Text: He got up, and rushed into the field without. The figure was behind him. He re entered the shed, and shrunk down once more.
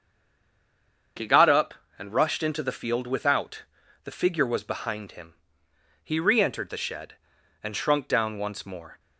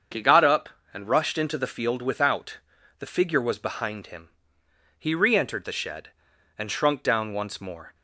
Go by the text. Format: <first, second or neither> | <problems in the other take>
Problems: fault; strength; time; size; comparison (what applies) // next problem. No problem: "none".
second | stays silent before the first word; until 1.1 s; 1.1 s long // starts louder than the rest; until 2.4 s; 7 dB; also in the second